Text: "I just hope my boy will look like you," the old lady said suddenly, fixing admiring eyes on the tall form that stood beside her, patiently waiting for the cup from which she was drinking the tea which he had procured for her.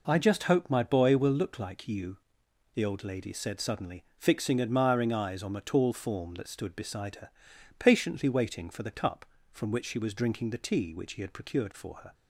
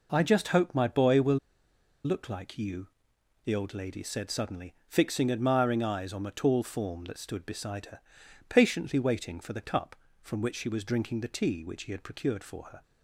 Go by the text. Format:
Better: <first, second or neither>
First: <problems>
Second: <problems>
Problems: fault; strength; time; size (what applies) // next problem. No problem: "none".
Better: first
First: none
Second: pauses between "will" and "look"; noticeable; at 1.3 s; 0.67 s long